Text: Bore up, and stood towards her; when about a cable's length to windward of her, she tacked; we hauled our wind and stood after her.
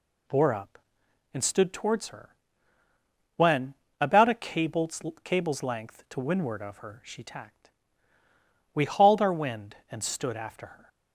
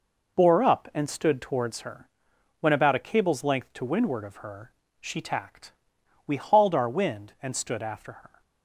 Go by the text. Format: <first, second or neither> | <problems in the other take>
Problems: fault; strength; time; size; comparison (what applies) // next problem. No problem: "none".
second | pauses between "when" and "about"; slight; at 3.7 s; 0.26 s long // says "cable's" twice; at 5.2 s